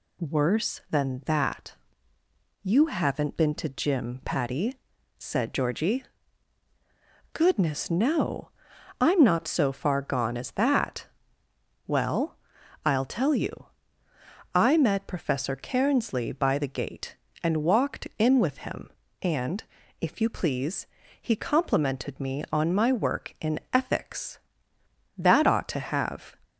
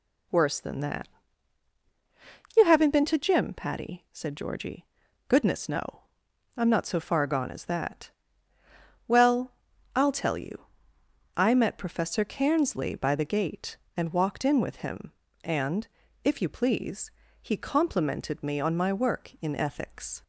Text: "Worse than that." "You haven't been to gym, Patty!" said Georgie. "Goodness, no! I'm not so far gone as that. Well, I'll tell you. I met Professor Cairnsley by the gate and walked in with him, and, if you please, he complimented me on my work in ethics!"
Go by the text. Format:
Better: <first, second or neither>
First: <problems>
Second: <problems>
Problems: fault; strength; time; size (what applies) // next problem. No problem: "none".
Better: second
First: goes on to say "That ought to have"; noticeable; from 25.1 s on; 1.2 s long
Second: none